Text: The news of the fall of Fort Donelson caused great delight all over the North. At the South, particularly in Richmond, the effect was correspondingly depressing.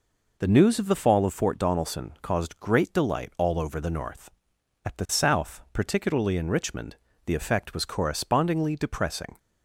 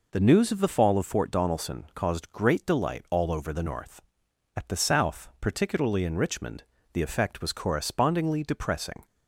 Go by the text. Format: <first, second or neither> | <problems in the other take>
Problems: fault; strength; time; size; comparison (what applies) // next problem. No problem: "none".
neither | none